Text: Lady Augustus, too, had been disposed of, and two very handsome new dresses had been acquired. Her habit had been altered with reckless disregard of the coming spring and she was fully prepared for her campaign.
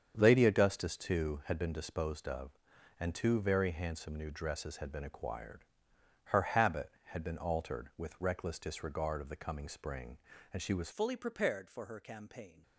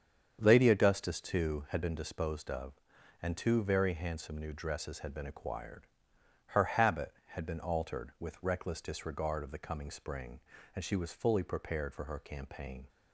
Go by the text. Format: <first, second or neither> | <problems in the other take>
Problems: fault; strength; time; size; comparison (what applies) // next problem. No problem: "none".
second | starts louder than the rest; strong; until 1.1 s; 7.5 dB; strong in the second // changes voice at "fully"; from 10.9 s on; 1.7 s long